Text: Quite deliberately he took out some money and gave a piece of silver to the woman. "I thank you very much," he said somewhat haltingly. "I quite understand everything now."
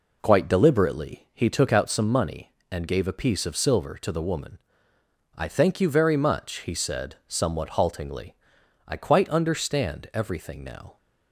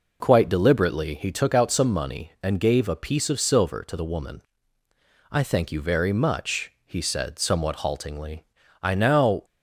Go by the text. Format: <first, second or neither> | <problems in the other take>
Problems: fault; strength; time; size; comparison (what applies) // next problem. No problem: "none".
first | skips "quite understand everything"; at 8.9 s